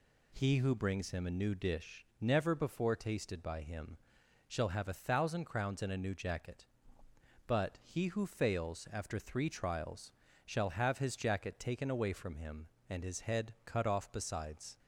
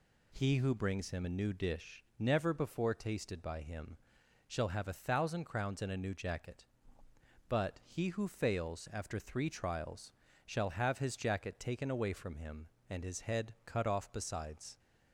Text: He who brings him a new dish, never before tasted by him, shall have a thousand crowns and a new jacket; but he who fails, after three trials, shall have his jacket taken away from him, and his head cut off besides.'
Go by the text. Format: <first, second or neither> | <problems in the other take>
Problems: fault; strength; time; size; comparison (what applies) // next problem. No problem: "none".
neither | none